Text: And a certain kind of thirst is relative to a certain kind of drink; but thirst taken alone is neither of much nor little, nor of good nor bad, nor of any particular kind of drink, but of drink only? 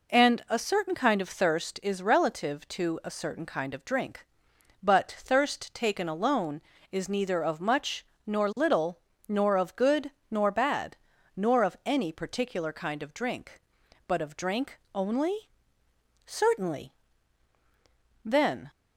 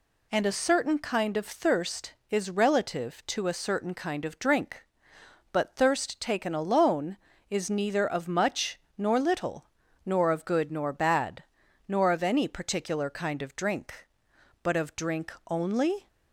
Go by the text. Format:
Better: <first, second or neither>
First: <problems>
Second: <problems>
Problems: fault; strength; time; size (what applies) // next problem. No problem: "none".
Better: second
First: pauses between "much" and "nor"; slight; at 8.0 s; 0.22 s long // pauses between "good" and "nor"; slight; at 10.1 s; 0.18 s long // pauses between "drink" and "only"; slight; at 14.7 s; 0.16 s long // goes on to say "Certainly Then"; strong; from 16.2 s on; 2.4 s long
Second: pauses between "much" and "nor"; slight; at 8.7 s; 0.20 s long // pauses between "drink" and "only"; slight; at 15.3 s; 0.20 s long